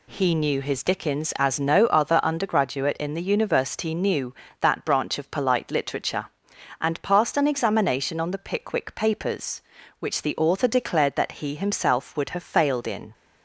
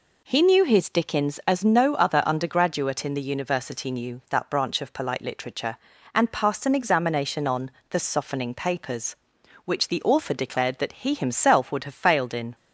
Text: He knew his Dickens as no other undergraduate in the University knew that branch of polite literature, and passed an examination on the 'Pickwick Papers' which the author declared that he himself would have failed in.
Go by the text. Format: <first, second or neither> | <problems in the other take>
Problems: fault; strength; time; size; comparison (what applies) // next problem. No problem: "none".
first | pauses between "on" and "the"; slight; at 7.7 s; 0.18 s long // says "Softening" for "Pickwick"; at 7.9 s